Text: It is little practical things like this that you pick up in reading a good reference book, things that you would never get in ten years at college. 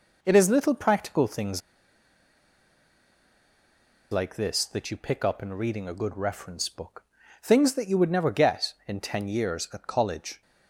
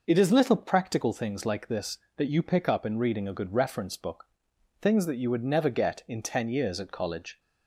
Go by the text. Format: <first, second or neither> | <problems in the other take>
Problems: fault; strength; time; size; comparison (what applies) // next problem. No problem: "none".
second | pauses between "things" and "like"; strong; at 1.6 s; 2.5 s long